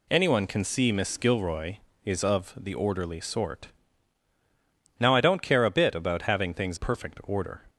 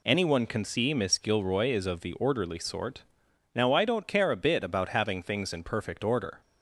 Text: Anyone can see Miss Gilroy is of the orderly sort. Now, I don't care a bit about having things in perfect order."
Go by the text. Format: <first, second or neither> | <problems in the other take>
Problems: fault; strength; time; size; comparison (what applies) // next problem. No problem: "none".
second | skips "in"; at 6.7 s